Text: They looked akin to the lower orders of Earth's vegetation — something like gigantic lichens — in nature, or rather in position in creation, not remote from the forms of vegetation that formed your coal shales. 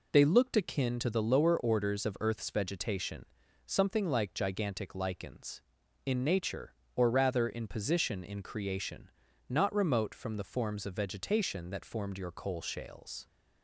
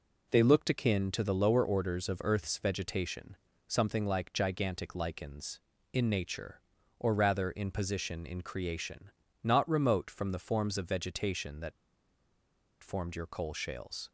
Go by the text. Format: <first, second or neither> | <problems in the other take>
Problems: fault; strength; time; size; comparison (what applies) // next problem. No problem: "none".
first | pauses between "that" and "formed"; at 11.7 s; 1.1 s long